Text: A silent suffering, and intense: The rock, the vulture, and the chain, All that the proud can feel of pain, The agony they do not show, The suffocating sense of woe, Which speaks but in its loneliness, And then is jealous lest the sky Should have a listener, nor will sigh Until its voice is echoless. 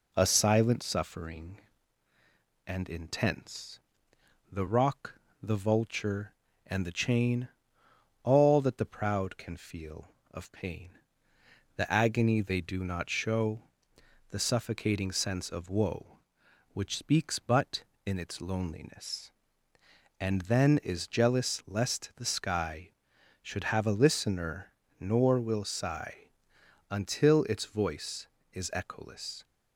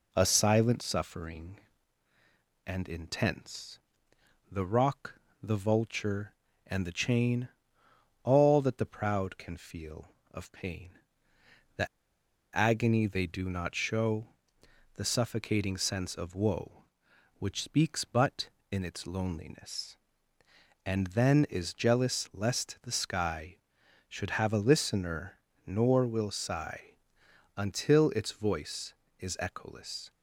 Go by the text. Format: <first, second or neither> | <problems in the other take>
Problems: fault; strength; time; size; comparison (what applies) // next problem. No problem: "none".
first | pauses between "The" and "agony"; noticeable; at 11.8 s; 0.67 s long // pauses between "sigh" and "Until"; noticeable; at 26.9 s; 0.66 s long; noticeable in the first